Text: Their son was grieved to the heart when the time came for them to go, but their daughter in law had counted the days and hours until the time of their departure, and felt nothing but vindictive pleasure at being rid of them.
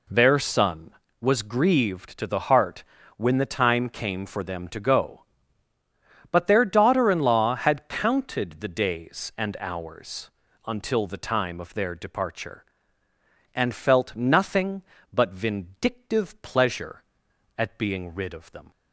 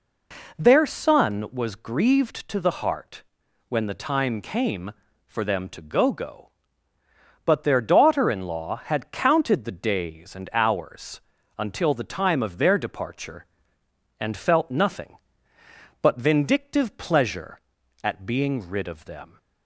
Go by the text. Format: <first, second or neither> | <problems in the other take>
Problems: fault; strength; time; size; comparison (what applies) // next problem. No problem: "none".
first | pauses between "heart" and "when"; at 3.2 s; 0.44 s long; slight in the first // says "go" twice; at 6.1 s // pauses between "hours" and "until"; at 11.1 s; 0.38 s long; slight in the first